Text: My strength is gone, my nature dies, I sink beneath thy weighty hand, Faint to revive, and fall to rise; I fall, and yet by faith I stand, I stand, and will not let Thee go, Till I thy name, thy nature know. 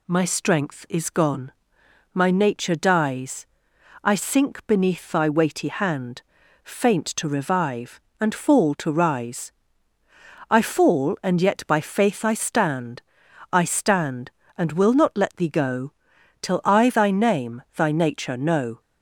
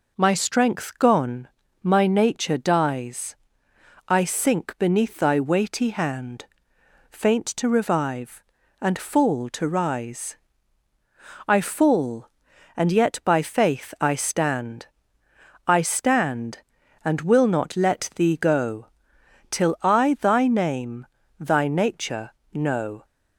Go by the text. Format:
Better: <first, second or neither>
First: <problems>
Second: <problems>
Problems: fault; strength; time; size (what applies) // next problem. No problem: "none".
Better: first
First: none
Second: skips "is"; at 0.9 s // pauses between "nature" and "know"; slight; at 22.3 s; 0.22 s long